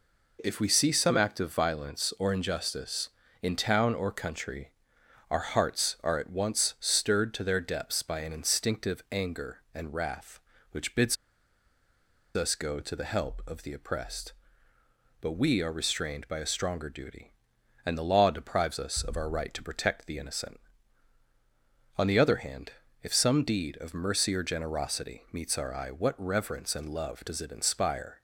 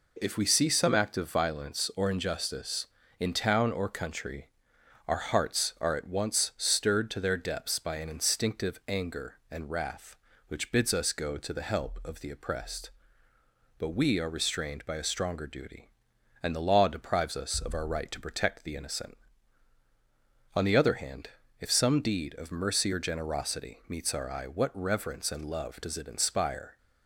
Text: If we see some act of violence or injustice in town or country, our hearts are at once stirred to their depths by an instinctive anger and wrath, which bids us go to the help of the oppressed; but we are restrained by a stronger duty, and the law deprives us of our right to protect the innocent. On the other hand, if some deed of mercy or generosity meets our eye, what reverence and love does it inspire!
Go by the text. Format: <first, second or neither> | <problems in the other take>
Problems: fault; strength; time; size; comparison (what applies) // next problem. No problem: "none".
second | pauses between "bids" and "us"; at 11.1 s; 1.2 s long